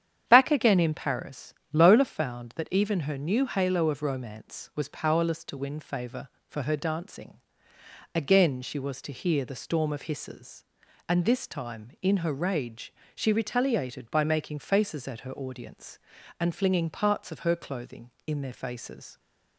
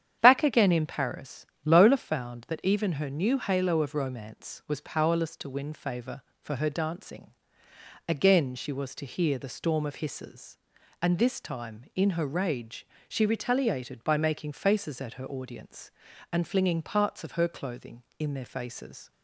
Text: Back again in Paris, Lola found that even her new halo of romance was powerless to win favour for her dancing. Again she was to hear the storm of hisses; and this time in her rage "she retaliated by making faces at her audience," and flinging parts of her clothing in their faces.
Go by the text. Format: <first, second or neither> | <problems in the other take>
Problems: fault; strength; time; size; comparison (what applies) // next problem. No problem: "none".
neither | starts louder than the rest; strong; the same in both // pauses between "rage" and "she"; slight; the same in both